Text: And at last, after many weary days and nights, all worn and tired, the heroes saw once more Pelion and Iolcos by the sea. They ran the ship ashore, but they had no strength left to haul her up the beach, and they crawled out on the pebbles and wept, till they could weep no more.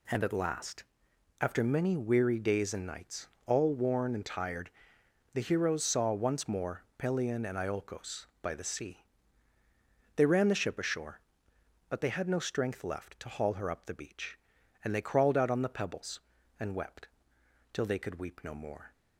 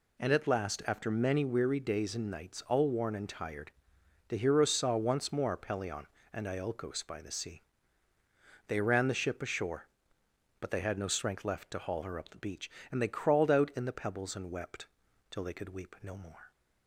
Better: first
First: none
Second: says "in" for "on"; at 13.7 s

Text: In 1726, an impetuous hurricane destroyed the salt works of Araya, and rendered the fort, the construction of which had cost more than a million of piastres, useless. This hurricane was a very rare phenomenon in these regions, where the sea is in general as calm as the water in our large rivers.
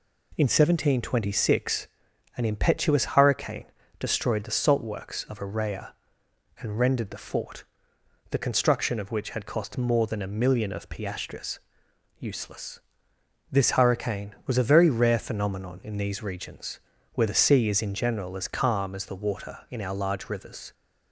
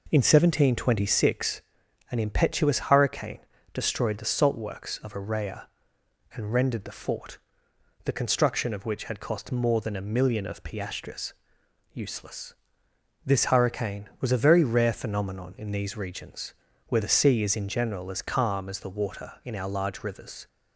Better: first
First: pauses between "hurricane" and "destroyed"; slight; at 3.6 s; 0.34 s long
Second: starts louder than the rest; noticeable; until 1.3 s; 4.5 dB // pauses between "hurricane" and "destroyed"; slight; at 3.3 s; 0.34 s long

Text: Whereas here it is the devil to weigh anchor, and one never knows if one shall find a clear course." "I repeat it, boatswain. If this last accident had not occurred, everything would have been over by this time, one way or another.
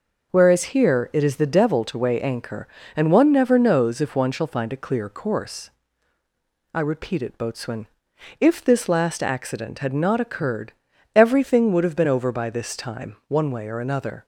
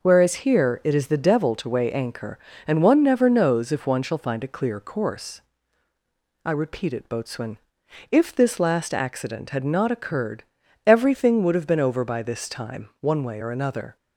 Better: neither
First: none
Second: none

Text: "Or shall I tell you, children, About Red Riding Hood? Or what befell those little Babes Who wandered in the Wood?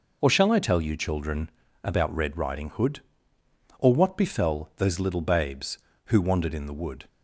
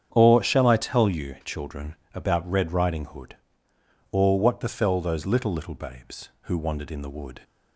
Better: first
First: none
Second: starts louder than the rest; strong; until 1.1 s; 8 dB // says "little" twice; at 5.5 s

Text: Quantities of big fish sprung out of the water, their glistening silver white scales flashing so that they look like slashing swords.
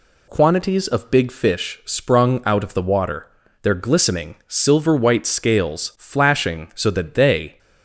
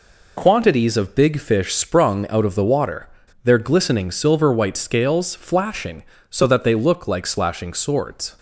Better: second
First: stops before "look like slashing swords"; at 7.5 s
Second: none

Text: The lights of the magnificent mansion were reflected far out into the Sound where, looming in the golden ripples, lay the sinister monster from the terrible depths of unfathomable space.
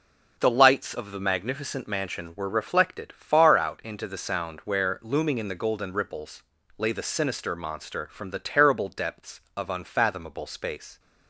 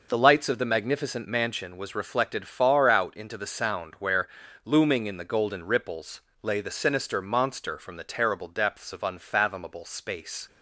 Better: first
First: none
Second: says "was" for "were"; at 1.7 s

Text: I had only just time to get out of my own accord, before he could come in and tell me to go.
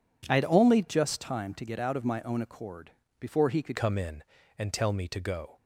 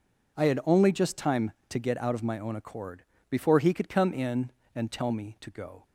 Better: second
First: changes voice at "come"; from 3.7 s on; 1.8 s long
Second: none

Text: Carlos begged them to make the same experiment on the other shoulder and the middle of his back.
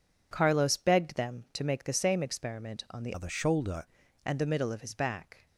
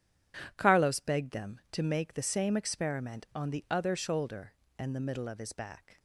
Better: second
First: changes voice from "other" to "shoulder"; from 3.1 to 3.8 s; 0.7 s long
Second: none

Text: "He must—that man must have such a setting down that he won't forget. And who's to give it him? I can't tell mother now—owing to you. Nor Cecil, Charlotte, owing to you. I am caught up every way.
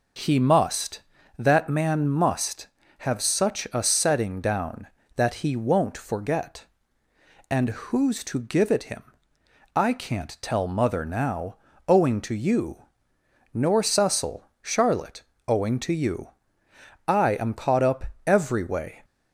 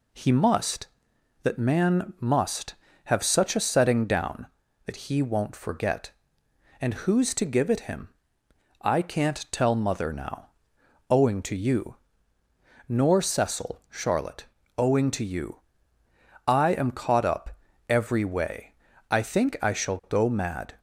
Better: first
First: pauses between "up" and "every"; slight; at 18.0 s; 0.18 s long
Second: pauses between "up" and "every"; slight; at 17.5 s; 0.32 s long // goes on to say "I think I shall go mad"; strong; from 19.0 s on; 1.6 s long

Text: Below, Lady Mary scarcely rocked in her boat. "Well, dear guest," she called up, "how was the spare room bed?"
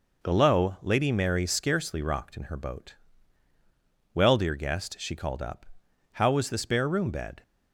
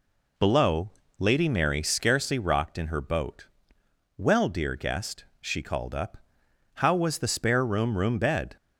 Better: first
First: none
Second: says "room" twice; at 7.9 s

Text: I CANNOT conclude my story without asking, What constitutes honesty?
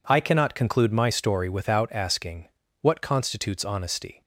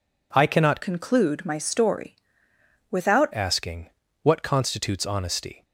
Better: first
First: none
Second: changes voice from "conclude" to "without"; from 0.8 to 3.2 s; 2.4 s long // pauses between "story" and "without"; noticeable; at 2.1 s; 0.74 s long

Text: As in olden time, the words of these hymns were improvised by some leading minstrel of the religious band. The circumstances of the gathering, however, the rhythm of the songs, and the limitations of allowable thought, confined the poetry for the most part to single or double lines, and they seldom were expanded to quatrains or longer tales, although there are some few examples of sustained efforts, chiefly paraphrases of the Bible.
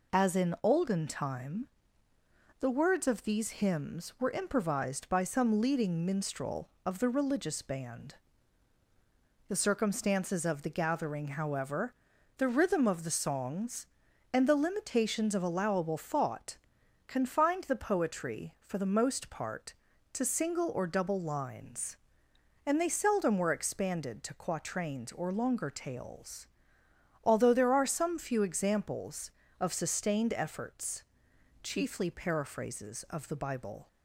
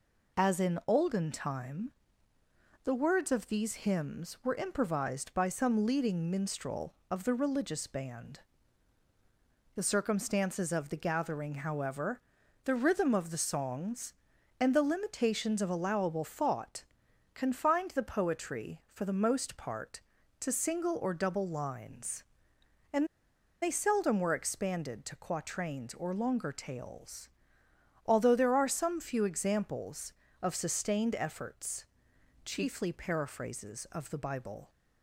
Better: first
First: none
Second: pauses between "and" and "they"; noticeable; at 23.0 s; 0.55 s long

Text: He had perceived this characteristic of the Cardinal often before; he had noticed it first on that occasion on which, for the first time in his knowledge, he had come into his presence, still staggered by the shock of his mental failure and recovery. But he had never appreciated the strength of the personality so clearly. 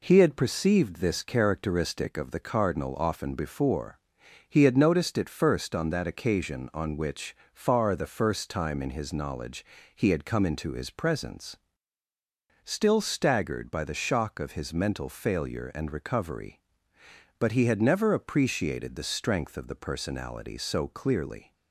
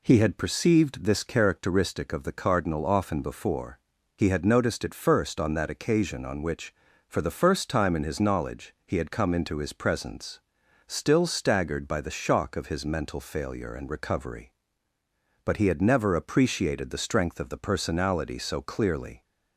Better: second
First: says "far" for "for"; at 7.5 s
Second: none

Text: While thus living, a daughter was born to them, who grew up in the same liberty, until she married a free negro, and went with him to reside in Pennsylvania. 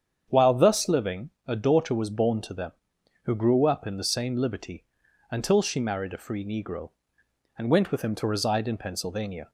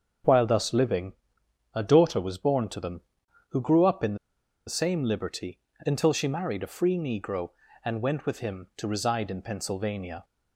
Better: first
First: starts louder than the rest; strong; until 1.3 s; 8 dB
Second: starts louder than the rest; until 1.8 s; 7 dB // pauses between "in" and "the"; noticeable; at 4.1 s; 0.51 s long

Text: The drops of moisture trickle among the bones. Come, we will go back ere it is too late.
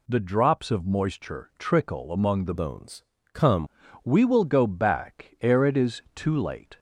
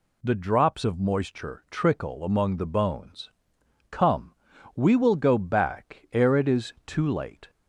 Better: second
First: changes voice from "bones" to "Come"; from 2.5 to 3.6 s; 1.1 s long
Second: none

